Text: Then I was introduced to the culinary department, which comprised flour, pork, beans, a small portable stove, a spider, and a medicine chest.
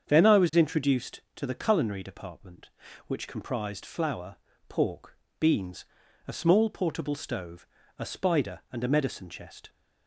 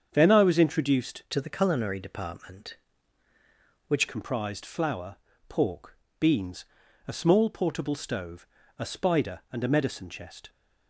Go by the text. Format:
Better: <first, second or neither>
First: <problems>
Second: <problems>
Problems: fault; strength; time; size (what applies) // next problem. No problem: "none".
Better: first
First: starts louder than the rest; strong; until 1.1 s; 7.5 dB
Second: starts louder than the rest; strong; until 1.1 s; 7.5 dB // changes voice from "to" to "which"; from 1.3 to 4.0 s; 2.7 s long